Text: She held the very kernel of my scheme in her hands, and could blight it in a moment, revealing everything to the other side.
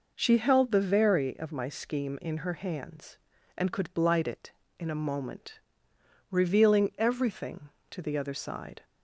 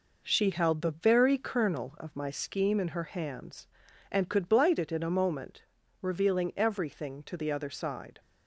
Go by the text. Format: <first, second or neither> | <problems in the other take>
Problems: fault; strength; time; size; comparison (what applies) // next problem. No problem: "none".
second | skips "kernel"; at 1.3 s